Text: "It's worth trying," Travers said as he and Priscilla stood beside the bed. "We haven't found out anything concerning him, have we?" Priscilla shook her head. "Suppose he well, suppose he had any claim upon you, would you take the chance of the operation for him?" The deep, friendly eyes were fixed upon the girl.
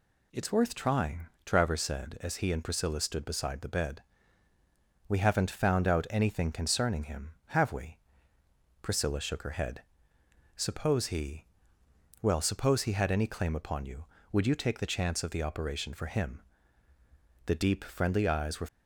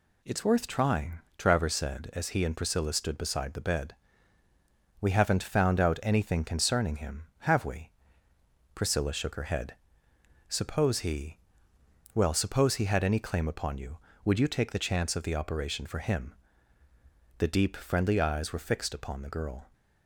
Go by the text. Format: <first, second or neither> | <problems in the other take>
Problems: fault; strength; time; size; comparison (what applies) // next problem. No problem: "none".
second | pauses between "he" and "well"; noticeable; at 11.4 s; 0.76 s long; noticeable in the second // stops before "fixed upon the girl"; at 18.6 s